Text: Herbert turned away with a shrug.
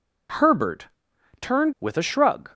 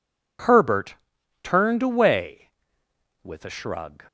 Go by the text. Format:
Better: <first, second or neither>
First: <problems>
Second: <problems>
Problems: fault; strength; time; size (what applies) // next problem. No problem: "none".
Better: second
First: pauses between "Herbert" and "turned"; noticeable; at 0.8 s; 0.54 s long // skips "away"; at 1.7 s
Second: pauses between "Herbert" and "turned"; noticeable; at 0.9 s; 0.48 s long